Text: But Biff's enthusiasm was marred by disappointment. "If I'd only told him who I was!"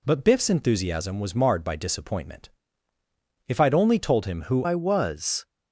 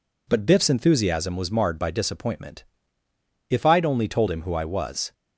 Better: second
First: changes voice at "I"; from 4.6 s on; 0.8 s long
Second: none

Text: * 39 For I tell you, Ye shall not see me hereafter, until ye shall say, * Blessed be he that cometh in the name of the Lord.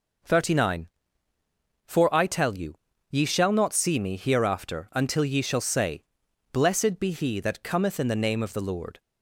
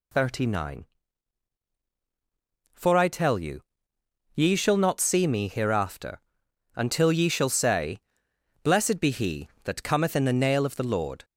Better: first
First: none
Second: says "nail" for "name"; at 10.3 s

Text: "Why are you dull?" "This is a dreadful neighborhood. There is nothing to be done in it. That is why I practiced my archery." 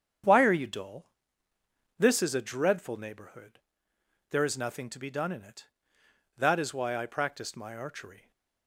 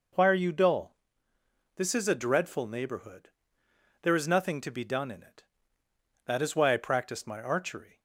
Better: second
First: gets quieter; strong; throughout; 8.5 dB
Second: none

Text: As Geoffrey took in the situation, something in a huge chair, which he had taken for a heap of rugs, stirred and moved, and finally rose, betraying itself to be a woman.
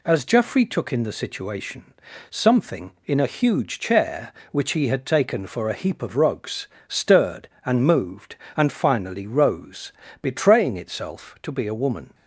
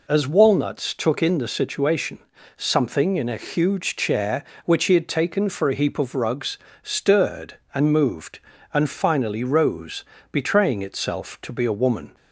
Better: first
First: none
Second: says "Walnuts" for "Geoffrey"; at 0.2 s

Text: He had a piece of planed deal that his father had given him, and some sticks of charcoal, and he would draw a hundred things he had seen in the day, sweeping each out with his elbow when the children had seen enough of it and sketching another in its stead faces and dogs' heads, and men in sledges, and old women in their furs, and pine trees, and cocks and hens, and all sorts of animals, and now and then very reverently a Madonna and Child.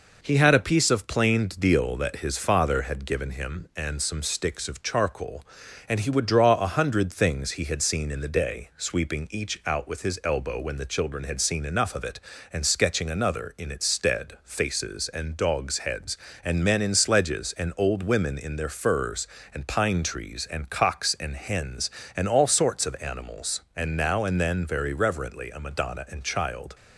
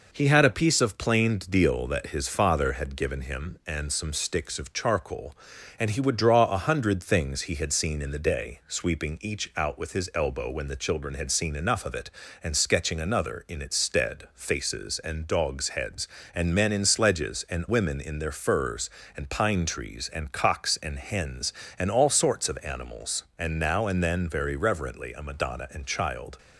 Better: first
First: none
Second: skips "old"; at 17.6 s

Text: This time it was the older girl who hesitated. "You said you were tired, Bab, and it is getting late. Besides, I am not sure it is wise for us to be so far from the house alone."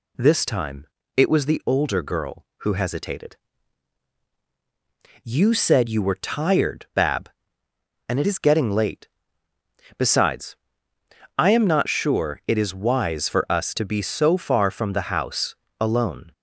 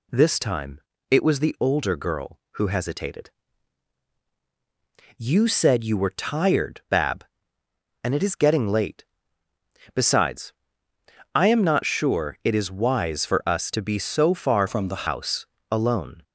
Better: first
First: pauses between "time" and "it"; slight; at 0.8 s; 0.32 s long // pauses between "house" and "alone"; slight; at 15.5 s; 0.26 s long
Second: pauses between "time" and "it"; slight; at 0.7 s; 0.32 s long // changes voice from "from" to "the"; from 14.6 to 15.0 s; 0.4 s long // pauses between "house" and "alone"; slight; at 15.4 s; 0.26 s long

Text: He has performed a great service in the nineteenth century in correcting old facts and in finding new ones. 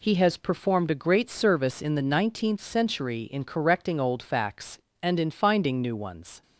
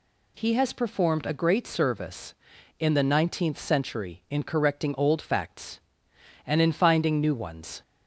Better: neither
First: none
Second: none

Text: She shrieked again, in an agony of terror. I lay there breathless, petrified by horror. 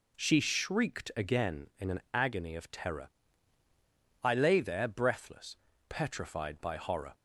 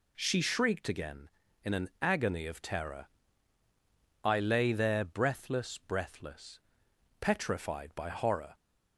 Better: first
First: none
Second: says "breathless" twice; at 5.7 s

